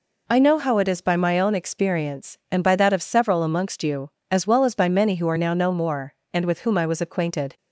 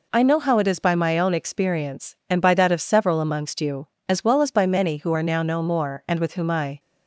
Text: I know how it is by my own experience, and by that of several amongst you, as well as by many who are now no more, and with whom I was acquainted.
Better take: first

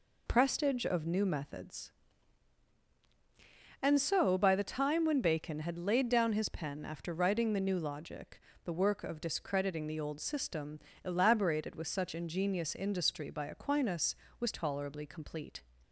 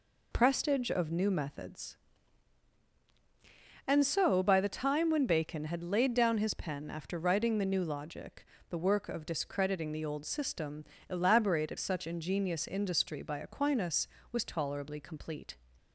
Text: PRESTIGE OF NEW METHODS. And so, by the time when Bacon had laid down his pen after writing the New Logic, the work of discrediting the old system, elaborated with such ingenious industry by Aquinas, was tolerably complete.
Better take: first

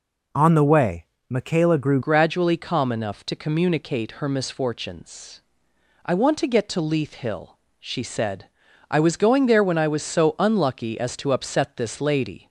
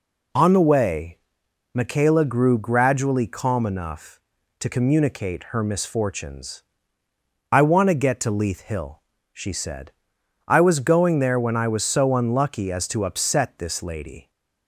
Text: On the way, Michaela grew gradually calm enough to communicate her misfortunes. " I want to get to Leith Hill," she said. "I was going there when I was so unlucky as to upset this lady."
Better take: second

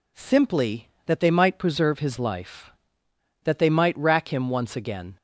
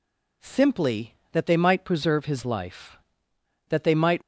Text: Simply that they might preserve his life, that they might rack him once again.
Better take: first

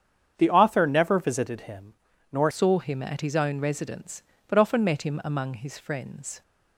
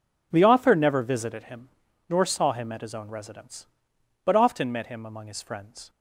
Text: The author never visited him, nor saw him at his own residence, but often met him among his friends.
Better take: second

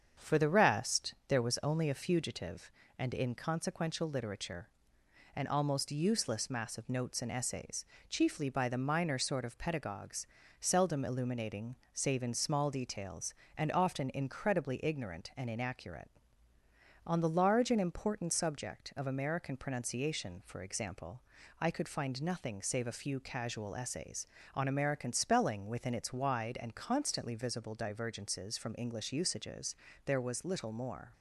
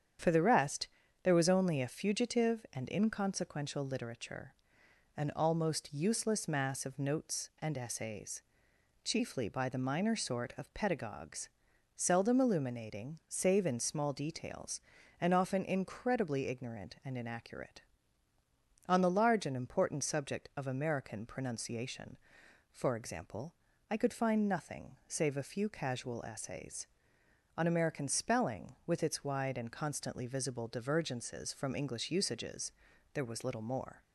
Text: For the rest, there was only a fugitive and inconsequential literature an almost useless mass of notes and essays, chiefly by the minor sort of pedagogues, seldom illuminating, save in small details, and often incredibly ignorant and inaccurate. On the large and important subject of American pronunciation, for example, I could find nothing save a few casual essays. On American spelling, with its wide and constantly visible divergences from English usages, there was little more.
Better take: second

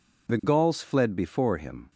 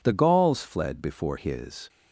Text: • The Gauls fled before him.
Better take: first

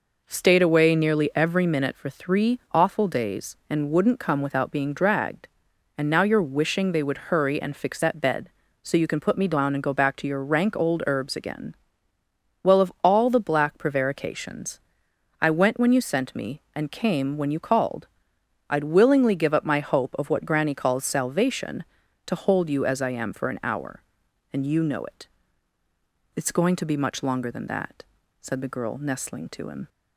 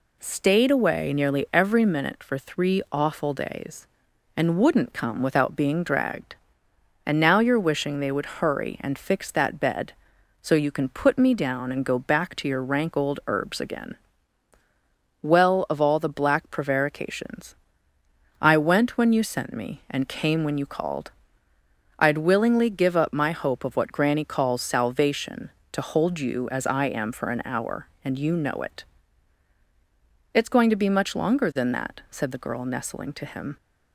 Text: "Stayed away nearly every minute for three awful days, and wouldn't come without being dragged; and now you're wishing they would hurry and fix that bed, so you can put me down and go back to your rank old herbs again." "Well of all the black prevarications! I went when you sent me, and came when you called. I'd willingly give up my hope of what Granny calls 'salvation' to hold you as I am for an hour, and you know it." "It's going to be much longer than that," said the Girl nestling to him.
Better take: neither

